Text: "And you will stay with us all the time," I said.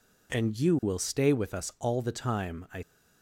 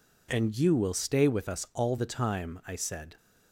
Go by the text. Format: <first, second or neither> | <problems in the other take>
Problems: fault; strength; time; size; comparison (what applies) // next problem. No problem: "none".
second | stops before "said"; at 2.8 s